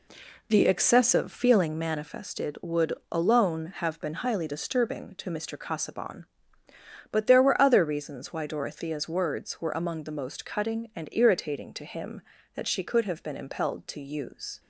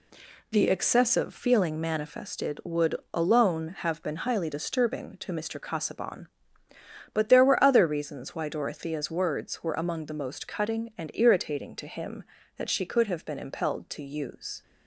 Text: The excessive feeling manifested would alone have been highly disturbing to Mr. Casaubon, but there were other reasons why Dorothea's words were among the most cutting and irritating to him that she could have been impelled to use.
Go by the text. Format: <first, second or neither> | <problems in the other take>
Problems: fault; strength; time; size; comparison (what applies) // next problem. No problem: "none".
second | starts louder than the rest; slight; until 1.7 s; 3 dB // pauses between "would" and "alone"; slight; at 2.9 s; 0.18 s long; slight in the second